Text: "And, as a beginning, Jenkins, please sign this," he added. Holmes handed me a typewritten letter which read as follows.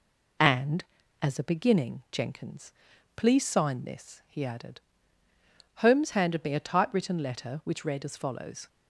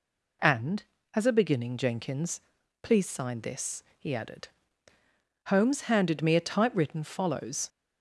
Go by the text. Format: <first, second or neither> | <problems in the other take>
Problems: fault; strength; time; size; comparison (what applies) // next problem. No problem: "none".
first | skips "letter which read as"; at 7.0 s